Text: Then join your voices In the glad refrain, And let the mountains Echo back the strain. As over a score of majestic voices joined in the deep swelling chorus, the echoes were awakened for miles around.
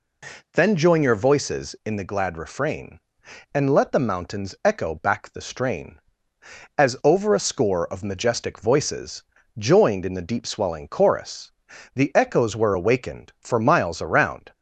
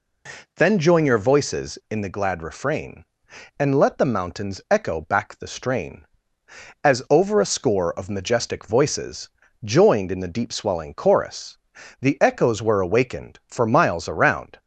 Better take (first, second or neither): neither